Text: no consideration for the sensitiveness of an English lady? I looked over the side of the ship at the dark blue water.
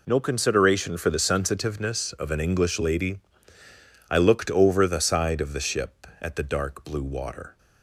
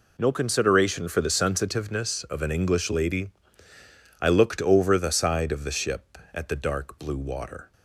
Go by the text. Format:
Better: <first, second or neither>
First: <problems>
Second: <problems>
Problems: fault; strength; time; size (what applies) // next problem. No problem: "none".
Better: neither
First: none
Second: none